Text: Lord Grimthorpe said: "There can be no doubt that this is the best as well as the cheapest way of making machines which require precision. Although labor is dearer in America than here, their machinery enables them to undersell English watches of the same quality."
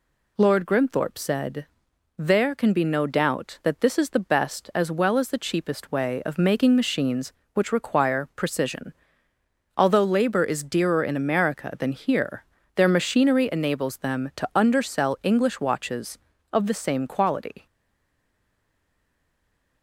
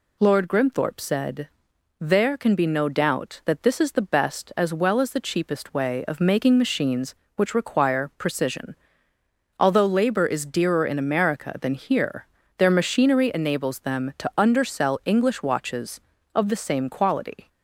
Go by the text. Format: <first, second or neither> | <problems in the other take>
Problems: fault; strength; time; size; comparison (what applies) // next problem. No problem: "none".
second | stays silent after the last word; from 17.6 s on; 2.2 s long